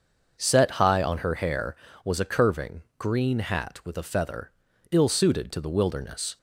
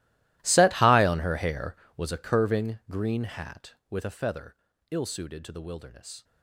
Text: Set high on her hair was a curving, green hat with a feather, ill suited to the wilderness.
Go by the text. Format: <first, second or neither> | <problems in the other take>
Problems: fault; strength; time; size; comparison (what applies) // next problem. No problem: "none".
first | gets quieter; strong; throughout; 21 dB // starts louder than the rest; strong; until 1.4 s; 16 dB; also in the first